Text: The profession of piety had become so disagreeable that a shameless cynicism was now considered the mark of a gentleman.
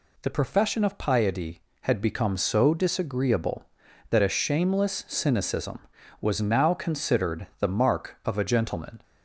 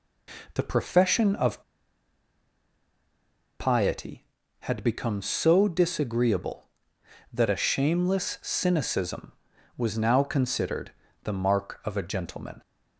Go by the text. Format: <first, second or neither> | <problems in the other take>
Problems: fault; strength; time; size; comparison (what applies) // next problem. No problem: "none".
first | pauses between "of" and "piety"; strong; at 1.6 s; 1.9 s long // pauses between "considered" and "the"; slight; at 10.9 s; 0.34 s long